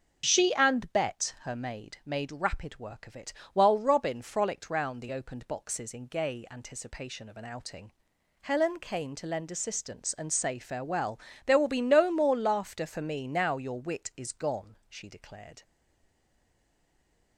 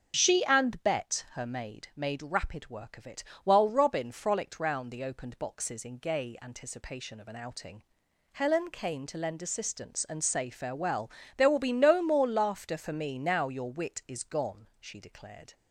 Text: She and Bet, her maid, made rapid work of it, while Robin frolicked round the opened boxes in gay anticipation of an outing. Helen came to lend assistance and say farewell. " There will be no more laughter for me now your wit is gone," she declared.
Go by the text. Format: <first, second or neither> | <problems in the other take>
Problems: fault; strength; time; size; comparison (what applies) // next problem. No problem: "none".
second | stays silent after the last word; noticeable; from 15.6 s on; 1.7 s long